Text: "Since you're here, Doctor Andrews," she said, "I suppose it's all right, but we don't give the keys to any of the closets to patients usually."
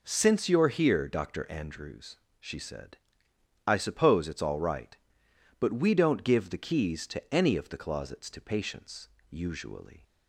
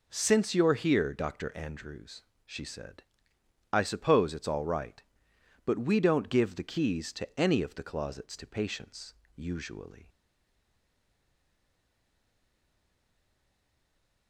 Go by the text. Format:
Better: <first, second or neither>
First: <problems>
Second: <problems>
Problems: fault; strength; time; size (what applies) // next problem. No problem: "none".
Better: first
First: pauses between "patients" and "usually"; slight; at 9.0 s; 0.24 s long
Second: pauses between "patients" and "usually"; slight; at 9.1 s; 0.24 s long // stays silent after the last word; strong; from 10.0 s on; 4.2 s long